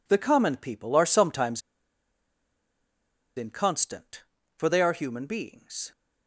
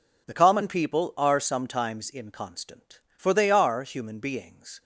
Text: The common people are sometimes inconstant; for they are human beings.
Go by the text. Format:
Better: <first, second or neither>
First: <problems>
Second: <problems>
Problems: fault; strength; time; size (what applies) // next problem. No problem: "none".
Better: second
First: pauses between "sometimes" and "inconstant"; strong; at 1.6 s; 1.7 s long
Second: none